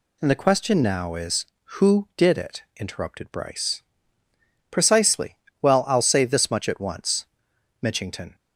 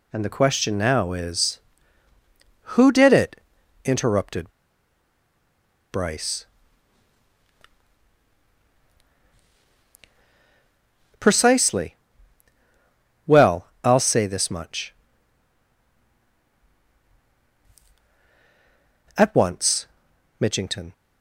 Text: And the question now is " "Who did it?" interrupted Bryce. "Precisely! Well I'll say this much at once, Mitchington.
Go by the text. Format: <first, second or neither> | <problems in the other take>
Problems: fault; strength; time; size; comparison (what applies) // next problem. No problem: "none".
first | pauses between "interrupted" and "Bryce"; strong; at 4.5 s; 1.4 s long // pauses between "Well" and "I'll"; slight; at 13.6 s; 0.16 s long